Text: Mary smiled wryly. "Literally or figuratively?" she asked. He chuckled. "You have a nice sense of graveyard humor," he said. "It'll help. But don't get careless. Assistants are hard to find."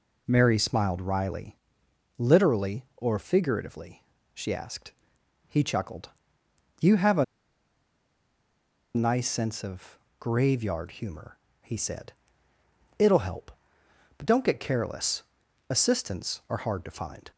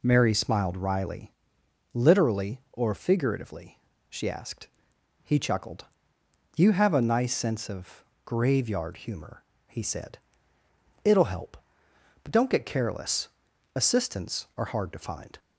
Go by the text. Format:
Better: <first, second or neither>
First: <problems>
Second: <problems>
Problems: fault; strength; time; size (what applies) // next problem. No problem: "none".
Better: second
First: pauses between "a" and "nice"; strong; at 7.2 s; 1.7 s long // pauses between "of" and "graveyard"; slight; at 9.9 s; 0.22 s long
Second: pauses between "of" and "graveyard"; slight; at 8.0 s; 0.22 s long